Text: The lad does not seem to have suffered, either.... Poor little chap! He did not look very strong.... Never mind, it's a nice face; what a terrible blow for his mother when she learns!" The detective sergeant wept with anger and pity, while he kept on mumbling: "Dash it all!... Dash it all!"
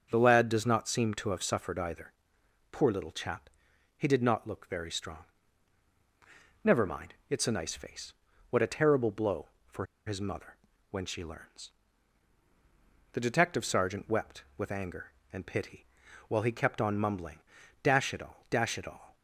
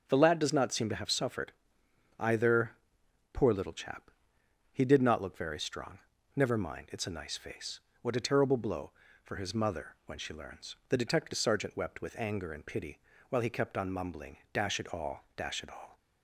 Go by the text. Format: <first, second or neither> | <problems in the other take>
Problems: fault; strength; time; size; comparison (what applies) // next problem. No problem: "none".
second | starts louder than the rest; until 1.1 s; 7 dB; also in the second // pauses between "for" and "his"; slight; at 9.8 s; 0.20 s long // pauses between "mother" and "when"; slight; at 10.5 s; 0.34 s long